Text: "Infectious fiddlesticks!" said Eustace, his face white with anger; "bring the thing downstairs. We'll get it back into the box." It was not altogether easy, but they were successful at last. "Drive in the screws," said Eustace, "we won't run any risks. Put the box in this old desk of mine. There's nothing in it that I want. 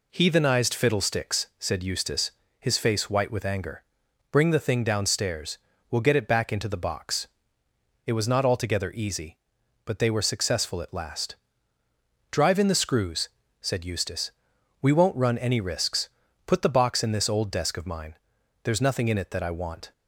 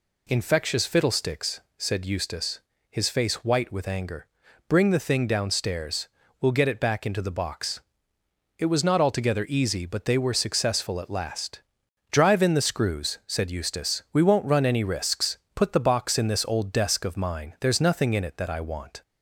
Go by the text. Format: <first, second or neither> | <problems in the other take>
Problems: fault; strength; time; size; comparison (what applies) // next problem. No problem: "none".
second | says "Heathenized" for "Infectious"; at 0.1 s